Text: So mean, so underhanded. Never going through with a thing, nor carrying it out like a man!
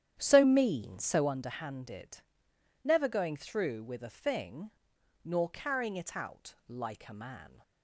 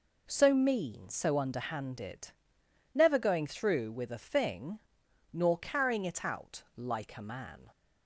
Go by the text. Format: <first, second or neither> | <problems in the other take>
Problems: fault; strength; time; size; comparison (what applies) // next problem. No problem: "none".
second | starts louder than the rest; strong; until 1.3 s; 10 dB